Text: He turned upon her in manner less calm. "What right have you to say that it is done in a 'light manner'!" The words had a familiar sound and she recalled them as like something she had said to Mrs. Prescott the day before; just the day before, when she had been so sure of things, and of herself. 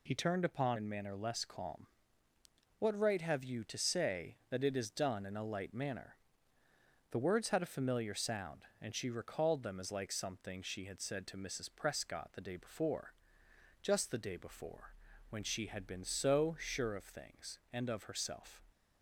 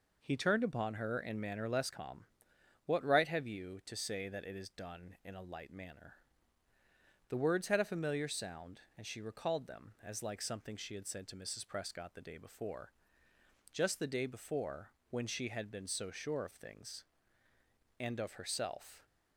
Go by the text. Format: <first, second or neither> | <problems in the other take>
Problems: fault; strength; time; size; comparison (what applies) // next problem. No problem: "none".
second | skips "her"; at 0.7 s